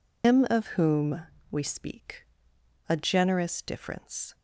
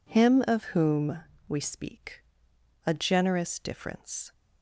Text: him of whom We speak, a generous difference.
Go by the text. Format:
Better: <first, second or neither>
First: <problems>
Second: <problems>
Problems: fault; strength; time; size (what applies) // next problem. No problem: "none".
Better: second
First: loses the start of "him"; at 0.2 s; 145 ms // pauses between "whom" and "We"; slight; at 1.2 s; 0.30 s long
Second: pauses between "whom" and "We"; slight; at 1.1 s; 0.30 s long